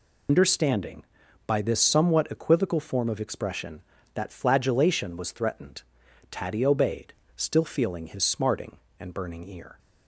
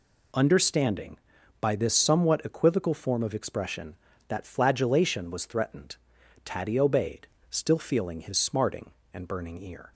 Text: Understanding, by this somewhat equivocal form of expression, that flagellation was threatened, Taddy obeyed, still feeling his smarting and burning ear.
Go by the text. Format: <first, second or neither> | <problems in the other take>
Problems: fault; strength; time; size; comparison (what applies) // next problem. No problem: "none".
second | loses the start of "Understanding"; at 0.2 s; 95 ms